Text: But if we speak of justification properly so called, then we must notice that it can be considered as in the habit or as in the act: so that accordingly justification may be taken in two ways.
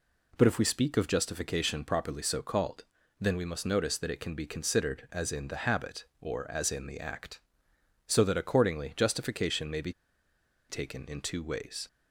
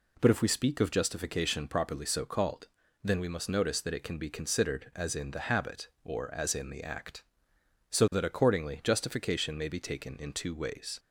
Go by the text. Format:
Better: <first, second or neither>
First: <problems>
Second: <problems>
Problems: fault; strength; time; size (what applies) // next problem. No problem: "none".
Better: second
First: pauses between "be" and "taken"; noticeable; at 9.9 s; 0.77 s long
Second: none